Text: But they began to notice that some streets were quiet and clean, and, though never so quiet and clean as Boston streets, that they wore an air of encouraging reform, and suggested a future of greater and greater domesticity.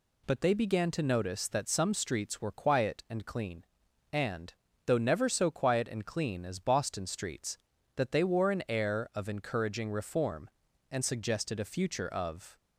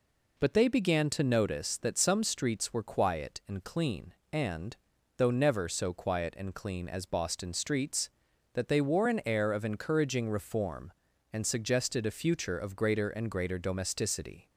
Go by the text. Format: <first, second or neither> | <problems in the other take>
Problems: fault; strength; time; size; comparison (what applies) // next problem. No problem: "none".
second | stops before "greater and greater domesticity"; at 12.5 s